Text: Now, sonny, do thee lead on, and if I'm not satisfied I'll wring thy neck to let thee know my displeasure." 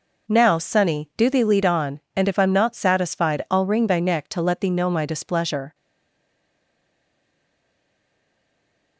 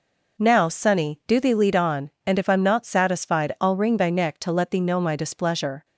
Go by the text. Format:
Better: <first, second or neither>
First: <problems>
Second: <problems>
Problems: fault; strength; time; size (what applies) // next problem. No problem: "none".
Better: second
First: stays silent after the last word; strong; from 5.7 s on; 3.2 s long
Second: none